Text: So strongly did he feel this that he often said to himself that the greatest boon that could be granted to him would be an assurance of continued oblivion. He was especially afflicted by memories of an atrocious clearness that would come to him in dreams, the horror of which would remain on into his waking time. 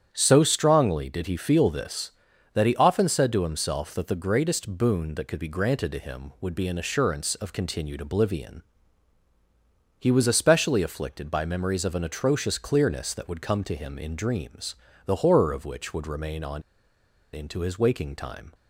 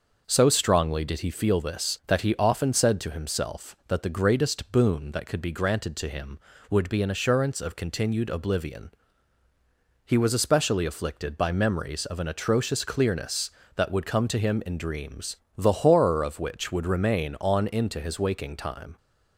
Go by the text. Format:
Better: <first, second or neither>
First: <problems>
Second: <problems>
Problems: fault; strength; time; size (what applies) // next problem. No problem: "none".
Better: second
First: starts louder than the rest; strong; until 1.1 s; 9 dB // pauses between "on" and "into"; noticeable; at 16.6 s; 0.72 s long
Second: starts louder than the rest; noticeable; until 1.2 s; 6 dB